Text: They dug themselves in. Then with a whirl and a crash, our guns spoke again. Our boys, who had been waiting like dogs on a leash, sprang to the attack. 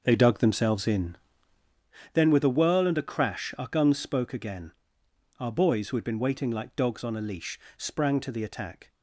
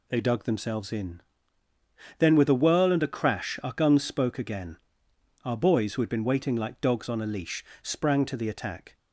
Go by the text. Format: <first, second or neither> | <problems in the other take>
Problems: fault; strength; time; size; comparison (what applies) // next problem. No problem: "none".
second | starts louder than the rest; until 2.0 s; 6 dB